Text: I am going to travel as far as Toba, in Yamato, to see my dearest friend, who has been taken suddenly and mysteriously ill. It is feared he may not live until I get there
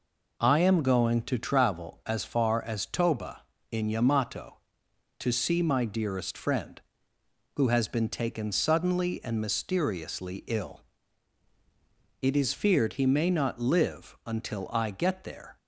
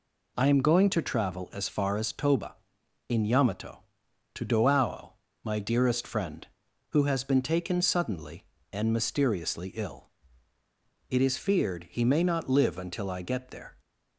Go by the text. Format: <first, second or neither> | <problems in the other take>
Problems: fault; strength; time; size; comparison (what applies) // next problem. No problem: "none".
first | says "doao" for "see"; at 4.4 s